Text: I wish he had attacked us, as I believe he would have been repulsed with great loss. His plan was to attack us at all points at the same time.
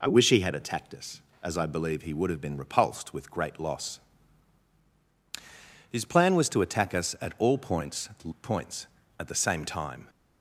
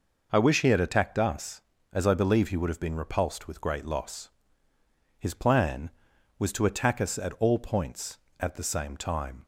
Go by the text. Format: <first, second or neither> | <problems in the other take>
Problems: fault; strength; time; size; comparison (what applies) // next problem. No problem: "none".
second | says "points" twice; at 8.4 s